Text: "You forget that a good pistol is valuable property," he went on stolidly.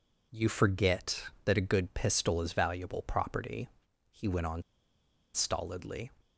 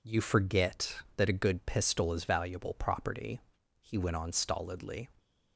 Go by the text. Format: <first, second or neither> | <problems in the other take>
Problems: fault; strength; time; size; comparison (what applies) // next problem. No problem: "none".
second | pauses between "on" and "stolidly"; noticeable; at 4.6 s; 0.72 s long